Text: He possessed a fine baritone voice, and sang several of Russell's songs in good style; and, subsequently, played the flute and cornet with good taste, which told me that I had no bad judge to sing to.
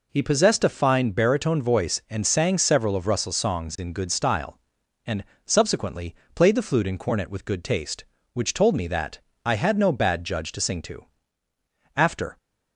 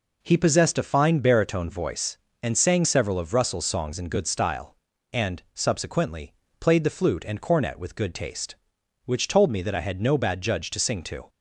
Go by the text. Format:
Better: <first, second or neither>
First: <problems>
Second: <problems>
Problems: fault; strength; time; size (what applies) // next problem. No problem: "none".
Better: second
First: pauses between "that" and "I"; slight; at 9.2 s; 0.22 s long // goes on to say "After"; slight; from 11.9 s on; 0.40 s long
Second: none